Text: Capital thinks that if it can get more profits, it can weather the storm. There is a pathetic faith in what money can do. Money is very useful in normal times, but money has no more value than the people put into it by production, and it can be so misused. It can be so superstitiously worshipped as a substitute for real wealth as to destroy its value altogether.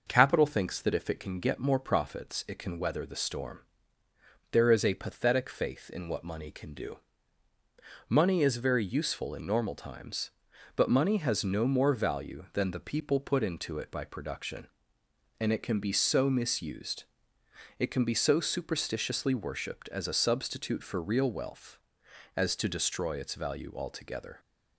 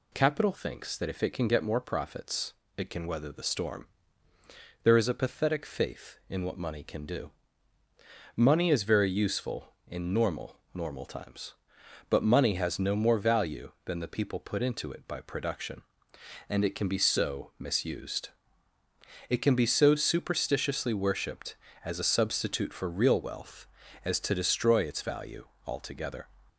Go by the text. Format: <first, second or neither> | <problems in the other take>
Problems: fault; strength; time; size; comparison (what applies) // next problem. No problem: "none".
first | says "normal" twice; at 10.7 s // pauses between "value" and "altogether"; slight; at 25.4 s; 0.20 s long